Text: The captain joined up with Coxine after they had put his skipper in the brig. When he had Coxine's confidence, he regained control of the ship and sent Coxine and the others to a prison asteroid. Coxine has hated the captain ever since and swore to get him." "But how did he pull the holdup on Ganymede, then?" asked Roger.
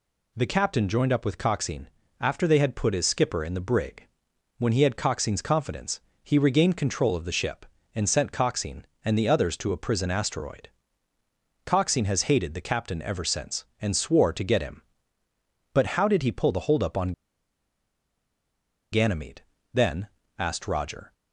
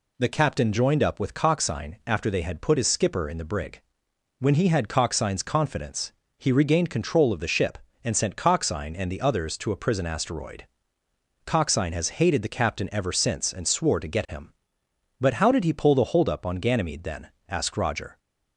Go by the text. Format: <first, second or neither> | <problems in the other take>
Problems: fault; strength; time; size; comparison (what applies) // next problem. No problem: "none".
second | pauses between "Coxine" and "after"; slight; at 1.8 s; 0.30 s long // pauses between "on" and "Ganymede"; strong; at 17.1 s; 1.7 s long